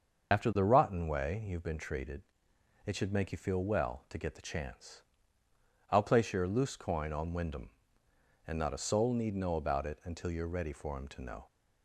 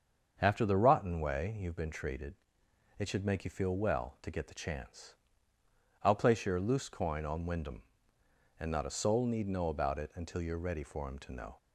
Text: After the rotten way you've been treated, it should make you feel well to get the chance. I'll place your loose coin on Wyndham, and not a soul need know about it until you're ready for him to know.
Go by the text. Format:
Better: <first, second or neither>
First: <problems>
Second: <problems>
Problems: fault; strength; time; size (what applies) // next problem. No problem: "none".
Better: second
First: loses the start of "After"; at 0.3 s; 70 ms // starts louder than the rest; until 1.3 s; 6.5 dB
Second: starts louder than the rest; until 1.3 s; 6.5 dB